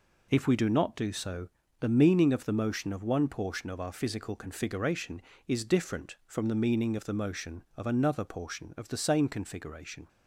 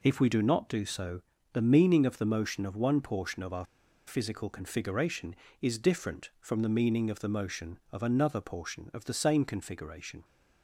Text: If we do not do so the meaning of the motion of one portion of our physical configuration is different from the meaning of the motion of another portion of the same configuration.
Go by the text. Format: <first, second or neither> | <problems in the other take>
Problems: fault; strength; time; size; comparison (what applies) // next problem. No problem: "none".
first | pauses between "so" and "the"; slight; at 1.2 s; 0.32 s long; slight in the first // pauses between "our" and "physical"; at 3.6 s; 0.41 s long